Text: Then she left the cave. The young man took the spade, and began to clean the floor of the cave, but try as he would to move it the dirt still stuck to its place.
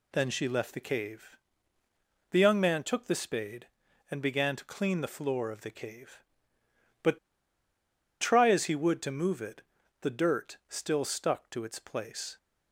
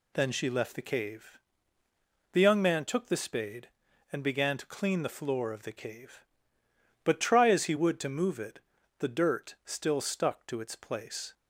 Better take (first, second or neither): second